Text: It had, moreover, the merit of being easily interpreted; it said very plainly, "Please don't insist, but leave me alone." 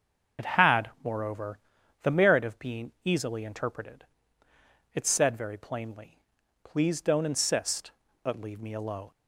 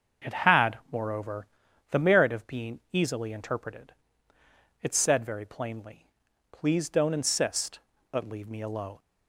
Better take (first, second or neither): second